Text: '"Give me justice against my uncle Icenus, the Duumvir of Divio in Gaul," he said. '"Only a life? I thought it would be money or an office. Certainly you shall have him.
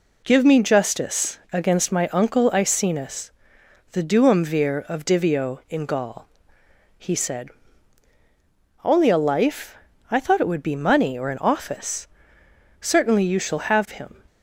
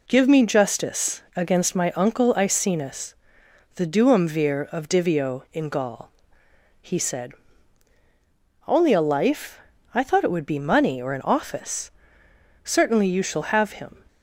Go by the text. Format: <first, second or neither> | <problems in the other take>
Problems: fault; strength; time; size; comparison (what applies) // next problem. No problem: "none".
neither | none